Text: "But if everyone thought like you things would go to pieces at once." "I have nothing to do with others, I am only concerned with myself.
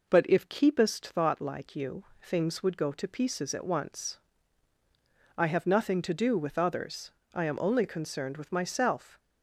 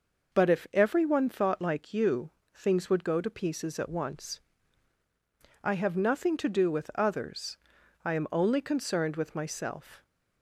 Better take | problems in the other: second | says "keepest" for "everyone"; at 0.4 s // pauses between "you" and "things"; slight; at 2.0 s; 0.18 s long; slight in the second

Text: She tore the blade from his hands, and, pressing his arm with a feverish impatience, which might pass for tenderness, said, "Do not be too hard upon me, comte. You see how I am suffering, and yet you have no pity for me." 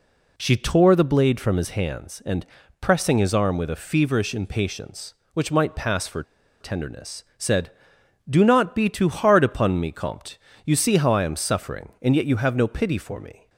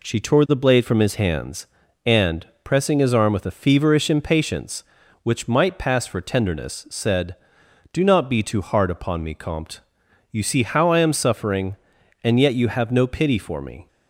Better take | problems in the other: second | pauses between "for" and "tenderness"; at 6.2 s; 0.38 s long

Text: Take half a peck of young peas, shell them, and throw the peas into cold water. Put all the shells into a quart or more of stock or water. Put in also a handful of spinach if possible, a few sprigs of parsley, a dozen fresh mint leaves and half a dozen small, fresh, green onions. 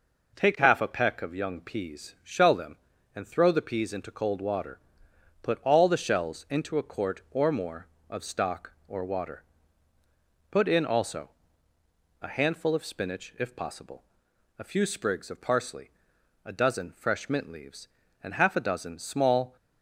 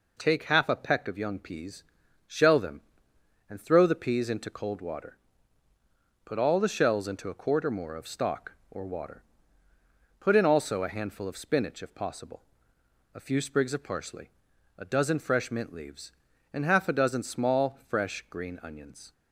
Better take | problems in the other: second | pauses between "also" and "a"; noticeable; at 11.2 s; 0.90 s long // stops before "fresh green onions"; at 19.5 s

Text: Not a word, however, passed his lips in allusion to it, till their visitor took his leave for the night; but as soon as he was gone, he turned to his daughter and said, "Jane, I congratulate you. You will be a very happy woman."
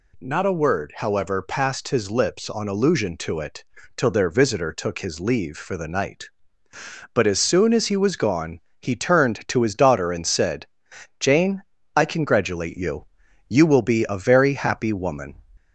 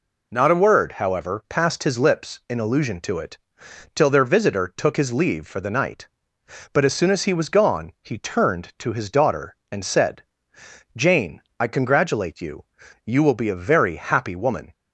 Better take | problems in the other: second | says "on" for "in"; at 2.4 s

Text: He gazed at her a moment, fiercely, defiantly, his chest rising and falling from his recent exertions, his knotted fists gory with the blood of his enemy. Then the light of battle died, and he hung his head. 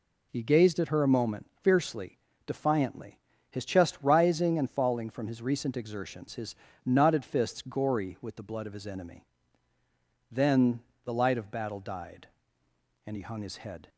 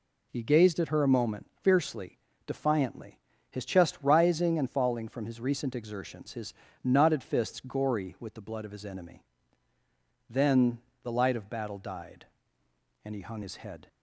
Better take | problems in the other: neither | pauses between "his" and "knotted"; slight; the same in both // pauses between "Then" and "the"; slight; the same in both

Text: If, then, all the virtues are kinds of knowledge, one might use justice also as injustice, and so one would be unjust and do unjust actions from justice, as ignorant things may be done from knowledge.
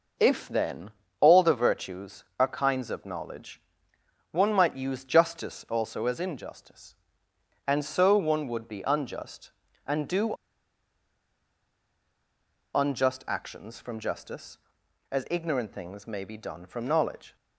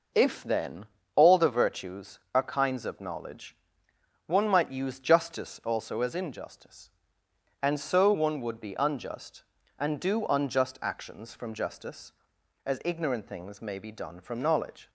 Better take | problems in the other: second | pauses between "do" and "unjust"; strong; at 10.3 s; 2.4 s long

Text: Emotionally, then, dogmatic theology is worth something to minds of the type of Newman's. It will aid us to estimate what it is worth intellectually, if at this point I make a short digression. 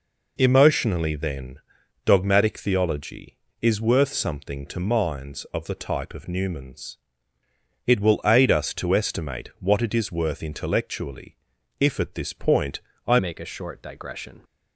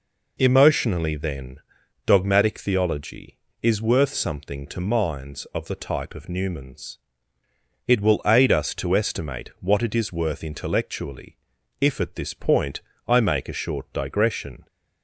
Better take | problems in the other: second | pauses between "point" and "I"; slight; at 12.8 s; 0.26 s long; slight in the second // changes voice at "make"; from 13.1 s on; 1.3 s long

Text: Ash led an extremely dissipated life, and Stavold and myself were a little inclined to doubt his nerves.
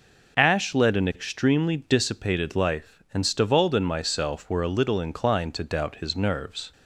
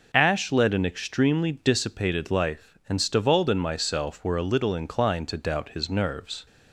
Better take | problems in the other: neither | none

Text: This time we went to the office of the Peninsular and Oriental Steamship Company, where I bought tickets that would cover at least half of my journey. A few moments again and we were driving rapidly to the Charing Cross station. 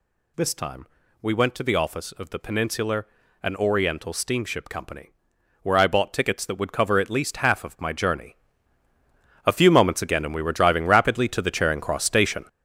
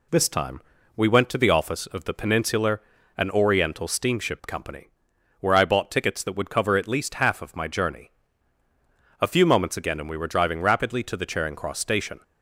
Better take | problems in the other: second | gets louder; strong; throughout; 8.5 dB // pauses between "time" and "we"; slight; at 0.8 s; 0.36 s long; slight in the second

